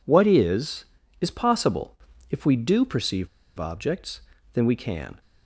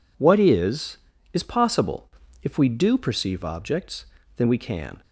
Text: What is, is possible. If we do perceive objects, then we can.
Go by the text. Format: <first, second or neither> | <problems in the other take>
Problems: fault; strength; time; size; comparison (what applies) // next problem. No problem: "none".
second | pauses between "perceive" and "objects"; slight; at 3.2 s; 0.30 s long